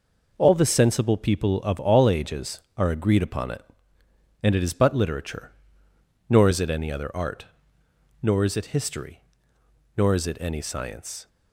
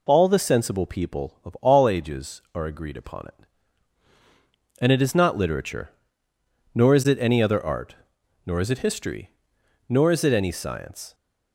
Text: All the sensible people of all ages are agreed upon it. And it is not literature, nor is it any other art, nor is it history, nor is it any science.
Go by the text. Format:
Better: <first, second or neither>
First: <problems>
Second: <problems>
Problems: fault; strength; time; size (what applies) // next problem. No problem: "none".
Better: second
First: says "but" for "not"; at 4.7 s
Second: none